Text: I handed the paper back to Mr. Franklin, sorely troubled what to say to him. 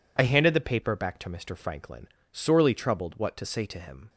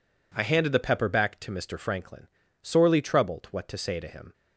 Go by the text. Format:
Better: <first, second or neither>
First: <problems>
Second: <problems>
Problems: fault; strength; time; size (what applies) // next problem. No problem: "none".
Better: first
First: none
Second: says "pepper" for "paper"; at 0.7 s